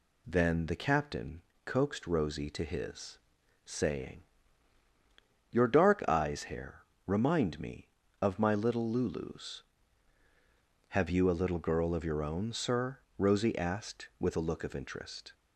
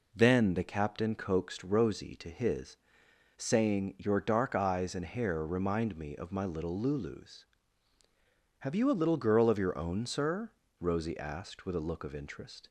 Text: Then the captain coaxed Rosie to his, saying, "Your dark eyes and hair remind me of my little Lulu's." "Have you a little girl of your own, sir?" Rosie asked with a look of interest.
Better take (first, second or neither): second